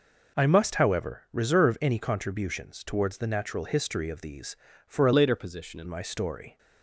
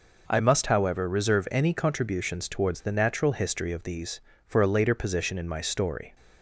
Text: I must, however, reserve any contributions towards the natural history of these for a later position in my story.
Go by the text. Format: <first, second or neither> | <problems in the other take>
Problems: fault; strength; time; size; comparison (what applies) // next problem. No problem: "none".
second | changes voice from "later" to "in"; from 5.1 to 5.8 s; 0.7 s long